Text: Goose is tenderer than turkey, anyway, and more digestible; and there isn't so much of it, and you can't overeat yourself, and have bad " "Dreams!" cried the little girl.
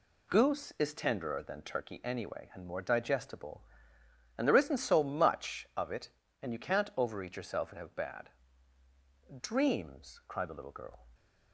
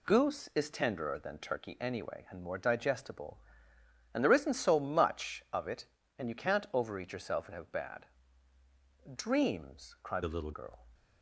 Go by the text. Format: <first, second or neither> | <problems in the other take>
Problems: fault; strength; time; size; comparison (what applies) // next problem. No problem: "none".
first | changes voice from "the" to "little"; from 10.2 to 10.5 s; 0.3 s long